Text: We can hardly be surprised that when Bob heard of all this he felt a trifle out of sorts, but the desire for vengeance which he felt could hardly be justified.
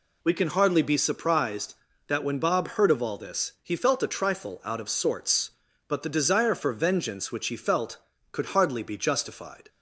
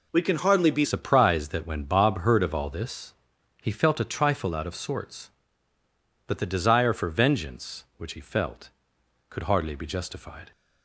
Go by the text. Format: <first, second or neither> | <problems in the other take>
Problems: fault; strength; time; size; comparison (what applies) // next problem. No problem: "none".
first | changes voice at "surprised"; from 0.8 s on; 9.7 s long // pauses between "this" and "he"; noticeable; at 3.1 s; 0.48 s long